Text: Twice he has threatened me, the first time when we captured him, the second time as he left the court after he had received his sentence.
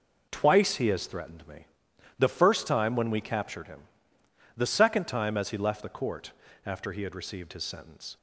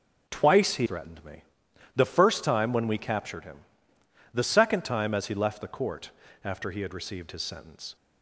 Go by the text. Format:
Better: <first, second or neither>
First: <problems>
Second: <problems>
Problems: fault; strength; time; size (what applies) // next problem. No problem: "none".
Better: first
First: pauses between "court" and "after"; slight; at 6.3 s; 0.32 s long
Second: starts louder than the rest; until 1.3 s; 6 dB // skips "has"; at 0.8 s // pauses between "court" and "after"; slight; at 6.1 s; 0.32 s long